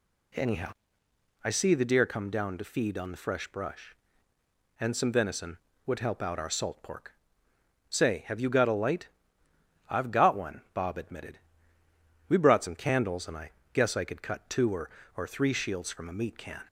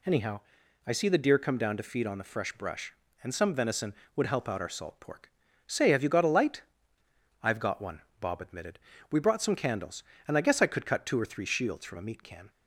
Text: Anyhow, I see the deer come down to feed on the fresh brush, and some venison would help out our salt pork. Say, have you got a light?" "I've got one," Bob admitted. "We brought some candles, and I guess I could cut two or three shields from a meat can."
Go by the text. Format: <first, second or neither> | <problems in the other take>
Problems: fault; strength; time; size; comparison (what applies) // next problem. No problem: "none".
second | pauses between "I" and "guess"; slight; at 13.5 s; 0.22 s long // says "or" twice; at 15.1 s